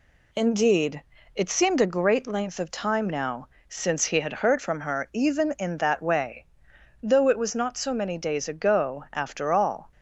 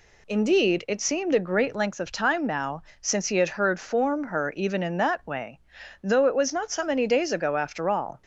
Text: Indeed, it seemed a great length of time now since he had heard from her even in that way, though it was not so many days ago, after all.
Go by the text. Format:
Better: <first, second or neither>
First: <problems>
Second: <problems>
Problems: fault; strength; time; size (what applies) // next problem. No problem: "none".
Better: first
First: pauses between "now" and "since"; slight; at 3.4 s; 0.18 s long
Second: pauses between "now" and "since"; slight; at 2.8 s; 0.20 s long // says "form" for "from"; at 3.7 s